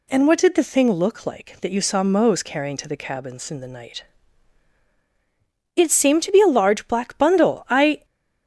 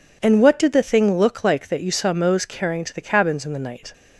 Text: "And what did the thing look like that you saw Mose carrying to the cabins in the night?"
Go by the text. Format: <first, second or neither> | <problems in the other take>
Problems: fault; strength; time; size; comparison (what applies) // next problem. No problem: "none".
second | goes on to say "It seemed to be a large black bundle I"; strong; from 5.7 s on; 2.3 s long